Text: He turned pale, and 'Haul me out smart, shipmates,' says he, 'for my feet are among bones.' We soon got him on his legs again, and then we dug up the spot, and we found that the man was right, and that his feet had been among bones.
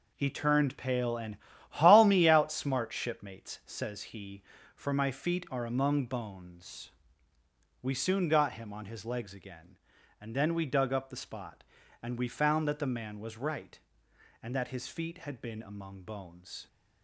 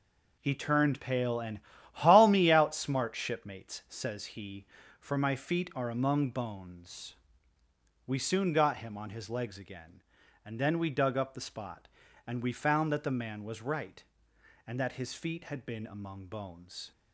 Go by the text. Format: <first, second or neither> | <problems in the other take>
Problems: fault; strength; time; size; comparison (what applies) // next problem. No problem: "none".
neither | pauses between "and" and "Haul"; slight; the same in both